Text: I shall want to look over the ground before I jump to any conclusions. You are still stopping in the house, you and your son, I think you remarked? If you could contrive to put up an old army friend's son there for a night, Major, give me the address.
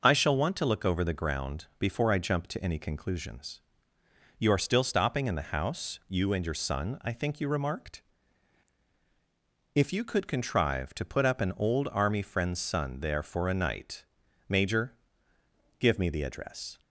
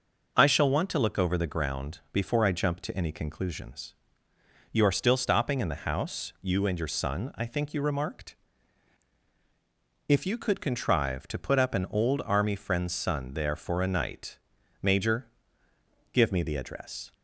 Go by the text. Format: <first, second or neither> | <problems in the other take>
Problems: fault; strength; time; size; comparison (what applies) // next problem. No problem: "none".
neither | none